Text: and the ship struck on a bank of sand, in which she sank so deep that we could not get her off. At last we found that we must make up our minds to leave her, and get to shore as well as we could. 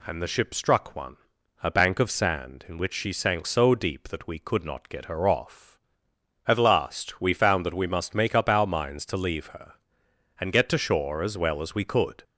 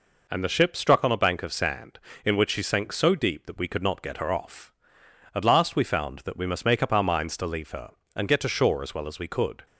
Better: second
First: says "one" for "on"; at 0.9 s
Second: none

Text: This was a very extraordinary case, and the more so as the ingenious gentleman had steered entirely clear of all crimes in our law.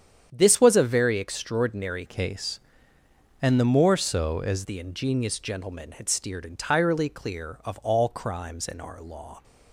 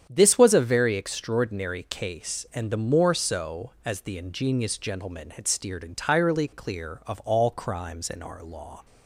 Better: second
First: starts louder than the rest; strong; until 1.3 s; 8.5 dB // changes voice from "case" to "as"; from 2.0 to 4.6 s; 2.6 s long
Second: starts louder than the rest; strong; until 1.1 s; 8.5 dB

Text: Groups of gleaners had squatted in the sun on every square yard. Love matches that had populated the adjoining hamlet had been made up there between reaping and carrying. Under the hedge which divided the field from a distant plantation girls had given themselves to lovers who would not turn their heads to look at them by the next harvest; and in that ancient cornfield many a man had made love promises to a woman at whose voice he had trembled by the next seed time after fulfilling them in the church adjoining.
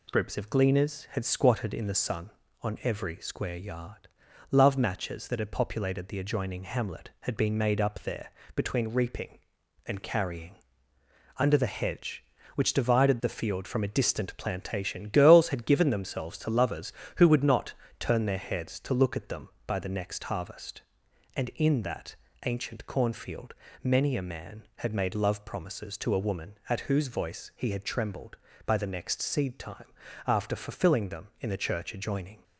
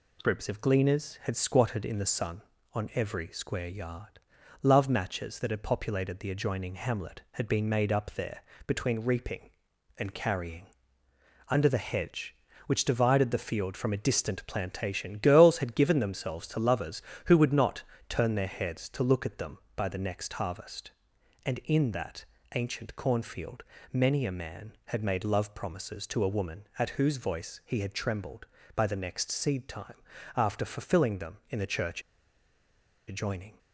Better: first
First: pauses between "there" and "between"; slight; at 8.3 s; 0.24 s long // pauses between "not" and "turn"; slight; at 17.7 s; 0.28 s long // pauses between "that" and "ancient"; slight; at 22.1 s; 0.28 s long // pauses between "cornfield" and "many"; slight; at 23.5 s; 0.28 s long // pauses between "time" and "after"; at 29.8 s; 0.40 s long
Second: pauses between "there" and "between"; slight; at 8.4 s; 0.24 s long // pauses between "not" and "turn"; slight; at 17.8 s; 0.28 s long // pauses between "that" and "ancient"; slight; at 22.2 s; 0.28 s long // pauses between "cornfield" and "many"; slight; at 23.6 s; 0.28 s long // pauses between "time" and "after"; at 29.9 s; 0.40 s long // pauses between "church" and "adjoining"; at 32.0 s; 1.0 s long

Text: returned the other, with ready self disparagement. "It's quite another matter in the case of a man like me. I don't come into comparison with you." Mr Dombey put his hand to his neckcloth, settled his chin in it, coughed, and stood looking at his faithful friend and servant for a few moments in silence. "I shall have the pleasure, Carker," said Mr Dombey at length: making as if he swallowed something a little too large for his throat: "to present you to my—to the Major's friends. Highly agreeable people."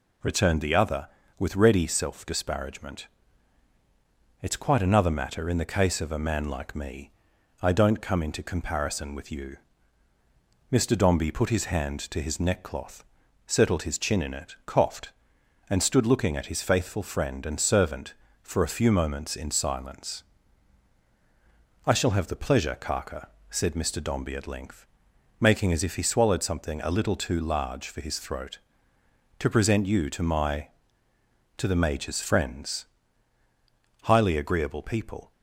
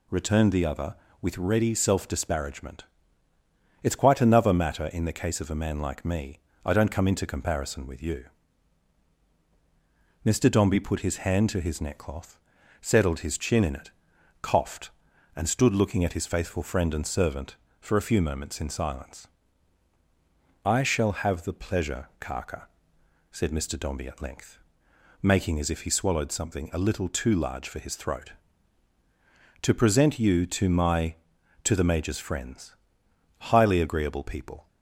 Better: neither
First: none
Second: none

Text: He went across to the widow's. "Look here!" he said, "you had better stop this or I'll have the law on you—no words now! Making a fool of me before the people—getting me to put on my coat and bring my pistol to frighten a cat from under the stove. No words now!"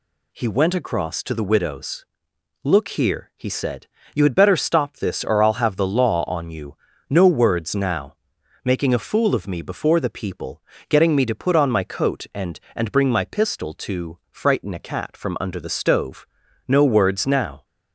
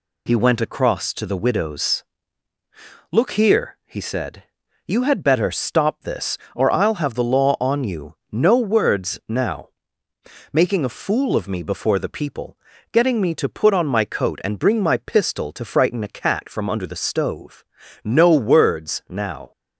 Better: second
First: says "and" twice; at 12.7 s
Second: none

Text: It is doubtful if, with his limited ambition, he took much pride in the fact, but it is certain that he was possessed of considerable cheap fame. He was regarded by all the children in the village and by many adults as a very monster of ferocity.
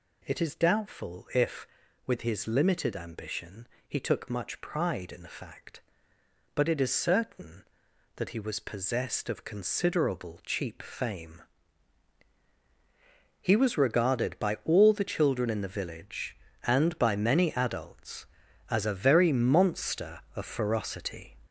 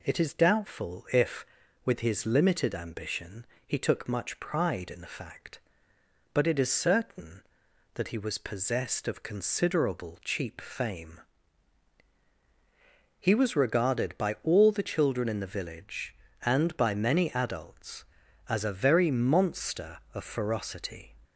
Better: second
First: gets louder; noticeable; throughout; 5.5 dB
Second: none

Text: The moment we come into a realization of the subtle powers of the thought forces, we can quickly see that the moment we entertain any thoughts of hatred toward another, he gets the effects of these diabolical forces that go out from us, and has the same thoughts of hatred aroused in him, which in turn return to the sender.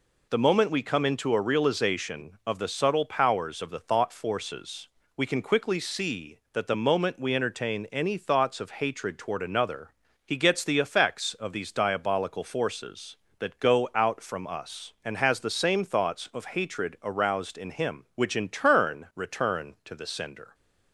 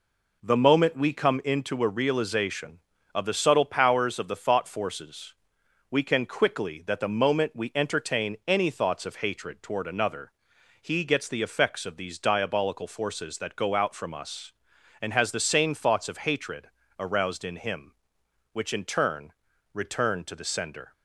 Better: first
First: none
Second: skips "see"; at 6.8 s // pauses between "hatred" and "aroused"; slight; at 16.6 s; 0.32 s long // pauses between "turn" and "return"; at 19.3 s; 0.40 s long

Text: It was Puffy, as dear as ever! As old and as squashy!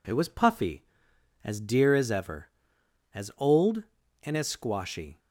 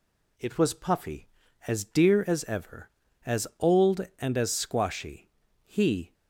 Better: first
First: none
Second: goes on to say "He"; from 5.6 s on; 0.50 s long

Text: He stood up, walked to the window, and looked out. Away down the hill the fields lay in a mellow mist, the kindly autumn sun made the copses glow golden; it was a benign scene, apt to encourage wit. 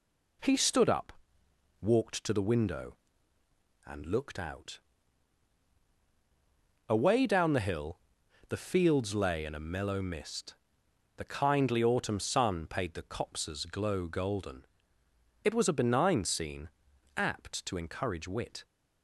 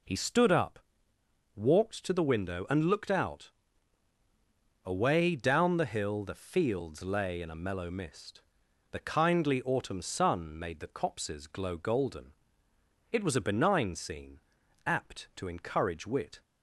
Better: second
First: pauses between "hill" and "the"; noticeable; at 7.9 s; 0.50 s long // says "paid" for "made"; at 12.6 s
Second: none

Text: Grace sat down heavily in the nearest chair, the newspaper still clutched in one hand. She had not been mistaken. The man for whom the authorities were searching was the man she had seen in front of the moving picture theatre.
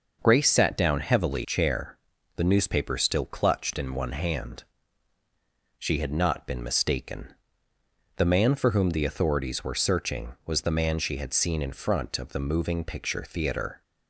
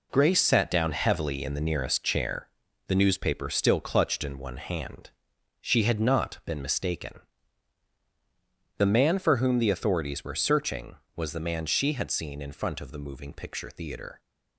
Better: second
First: starts louder than the rest; noticeable; until 1.2 s; 6 dB // skips "in the nearest"; at 1.4 s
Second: none

